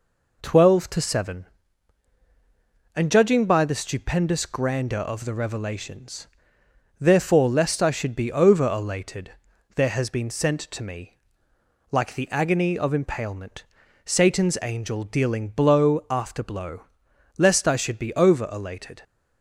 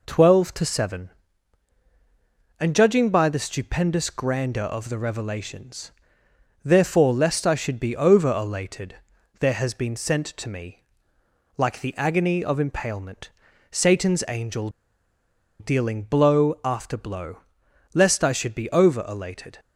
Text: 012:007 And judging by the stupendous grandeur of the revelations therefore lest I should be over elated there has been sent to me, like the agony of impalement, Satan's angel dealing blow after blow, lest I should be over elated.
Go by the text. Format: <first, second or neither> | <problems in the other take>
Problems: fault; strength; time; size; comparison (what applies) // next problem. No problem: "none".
first | pauses between "revelations" and "therefore"; noticeable; at 5.9 s; 0.74 s long; noticeable in the first // pauses between "elated" and "there"; at 8.9 s; 0.44 s long; also in the first // pauses between "angel" and "dealing"; noticeable; at 14.6 s; 0.90 s long